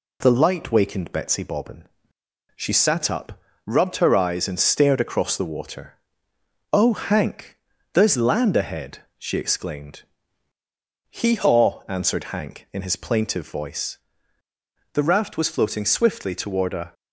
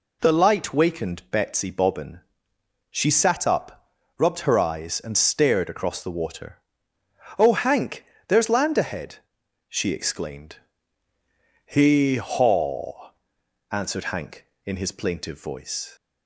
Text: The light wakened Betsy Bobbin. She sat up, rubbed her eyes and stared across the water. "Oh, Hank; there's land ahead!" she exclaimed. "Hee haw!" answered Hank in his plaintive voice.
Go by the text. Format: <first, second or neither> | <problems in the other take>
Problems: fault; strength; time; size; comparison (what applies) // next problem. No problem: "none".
second | goes on to say "The raft was floating swiftly toward a"; strong; from 14.9 s on; 2.0 s long